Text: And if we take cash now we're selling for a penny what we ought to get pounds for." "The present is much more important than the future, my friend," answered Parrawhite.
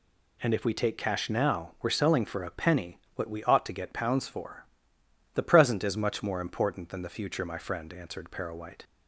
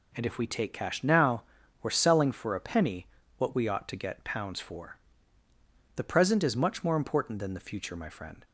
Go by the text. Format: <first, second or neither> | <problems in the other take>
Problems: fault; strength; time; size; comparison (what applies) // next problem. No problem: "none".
first | pauses between "now" and "we're"; at 1.4 s; 0.38 s long // pauses between "penny" and "what"; slight; at 3.0 s; 0.30 s long; slight in the first // stops before "answered Parrawhite"; at 8.4 s